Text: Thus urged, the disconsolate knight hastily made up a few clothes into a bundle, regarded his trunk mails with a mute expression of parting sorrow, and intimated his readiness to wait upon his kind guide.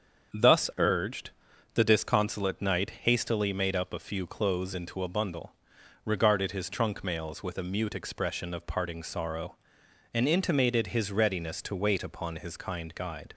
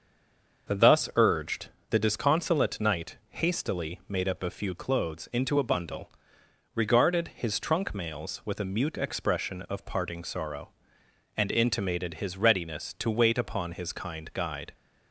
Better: first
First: starts louder than the rest; strong; until 1.8 s; 7 dB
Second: stays silent before the first word; slight; until 0.6 s; 0.6 s long // starts louder than the rest; until 1.9 s; 6.5 dB

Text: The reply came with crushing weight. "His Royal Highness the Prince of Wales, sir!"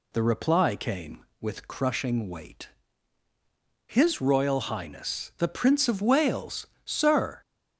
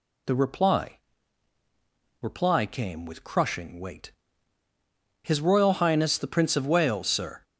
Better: first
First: none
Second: says "reply" twice; at 2.2 s

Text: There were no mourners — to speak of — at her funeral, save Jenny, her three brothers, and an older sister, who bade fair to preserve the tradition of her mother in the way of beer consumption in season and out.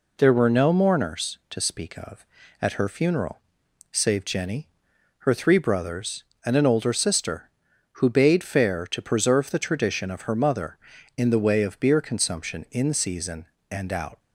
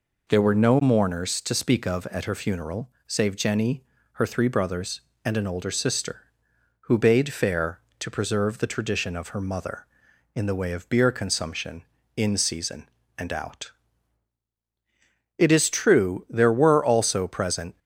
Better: first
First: none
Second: goes on to say "It is true there were also present"; strong; from 15.3 s on; 2.4 s long

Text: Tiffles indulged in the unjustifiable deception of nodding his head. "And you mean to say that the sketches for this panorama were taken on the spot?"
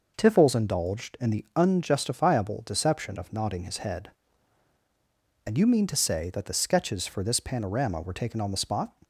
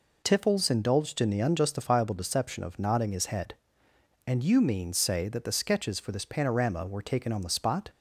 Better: first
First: none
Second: skips "to"; at 4.9 s

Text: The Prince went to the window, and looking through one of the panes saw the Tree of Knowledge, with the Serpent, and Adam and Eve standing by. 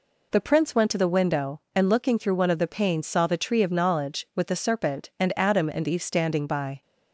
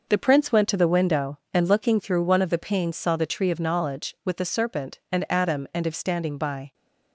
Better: first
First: none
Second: gets quieter; strong; throughout; 7.5 dB

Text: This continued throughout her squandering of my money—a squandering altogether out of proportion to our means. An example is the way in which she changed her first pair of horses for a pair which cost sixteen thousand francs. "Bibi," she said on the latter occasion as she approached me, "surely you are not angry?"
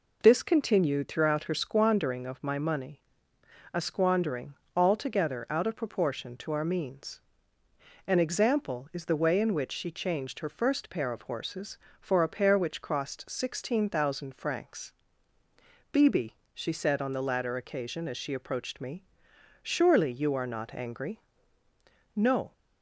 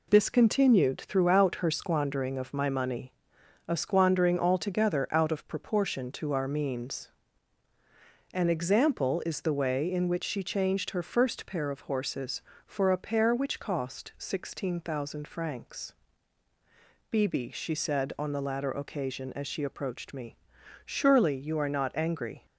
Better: second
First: pauses between "squandering" and "altogether"; slight; at 4.5 s; 0.22 s long // goes on to say "No"; slight; from 22.1 s on; 0.38 s long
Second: none

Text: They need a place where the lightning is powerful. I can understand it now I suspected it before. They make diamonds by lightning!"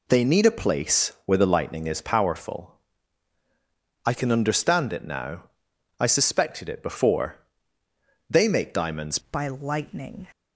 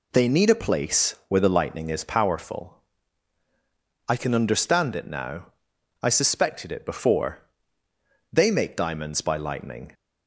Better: second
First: pauses between "now" and "I"; noticeable; at 5.4 s; 0.56 s long // changes voice at "by"; from 9.3 s on; 0.9 s long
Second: pauses between "now" and "I"; noticeable; at 5.4 s; 0.56 s long

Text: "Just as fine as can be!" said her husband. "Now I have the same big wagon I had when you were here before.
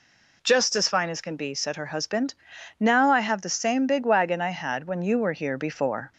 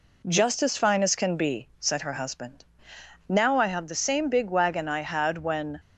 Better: first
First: none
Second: stops before "you were here before"; at 5.7 s

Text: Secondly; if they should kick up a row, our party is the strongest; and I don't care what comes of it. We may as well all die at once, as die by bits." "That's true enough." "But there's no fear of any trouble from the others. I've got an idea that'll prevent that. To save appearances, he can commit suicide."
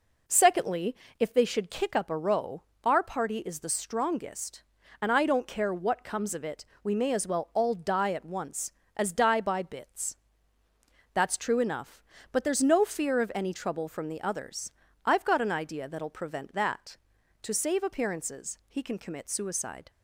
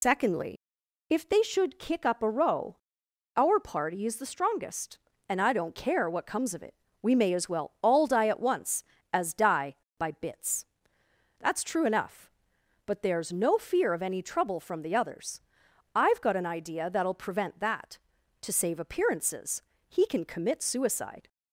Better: first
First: none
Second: loses the start of "Secondly"; at 0.0 s; 95 ms

